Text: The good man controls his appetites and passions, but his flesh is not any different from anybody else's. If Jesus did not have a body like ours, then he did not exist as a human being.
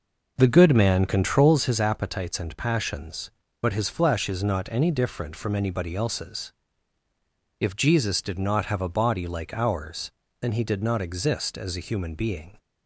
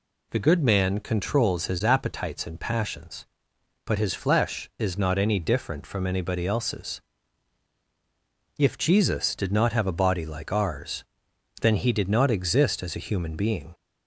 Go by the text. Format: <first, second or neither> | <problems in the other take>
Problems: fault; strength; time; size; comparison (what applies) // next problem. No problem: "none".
second | starts louder than the rest; noticeable; until 1.6 s; 5.5 dB